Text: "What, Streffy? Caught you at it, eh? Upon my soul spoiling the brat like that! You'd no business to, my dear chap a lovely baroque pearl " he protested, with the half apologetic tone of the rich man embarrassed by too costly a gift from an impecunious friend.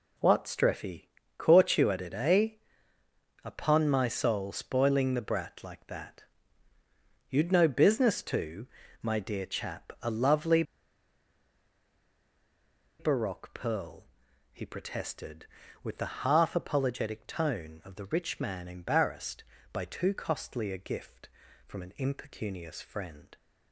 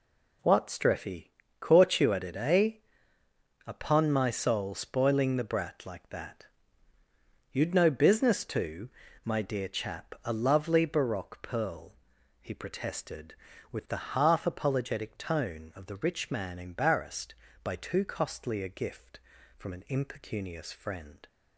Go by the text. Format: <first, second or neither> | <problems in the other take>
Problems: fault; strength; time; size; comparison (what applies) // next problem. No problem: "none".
second | pauses between "lovely" and "baroque"; strong; at 10.6 s; 2.3 s long